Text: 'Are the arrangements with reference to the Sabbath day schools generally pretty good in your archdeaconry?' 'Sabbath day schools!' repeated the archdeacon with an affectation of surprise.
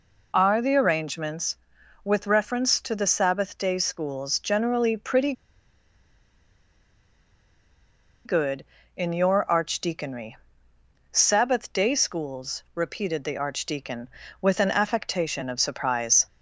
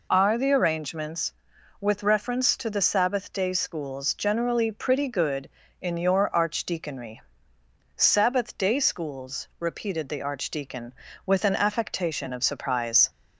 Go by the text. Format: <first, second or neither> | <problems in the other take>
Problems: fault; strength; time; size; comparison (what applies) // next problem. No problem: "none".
second | pauses between "pretty" and "good"; strong; at 5.3 s; 2.9 s long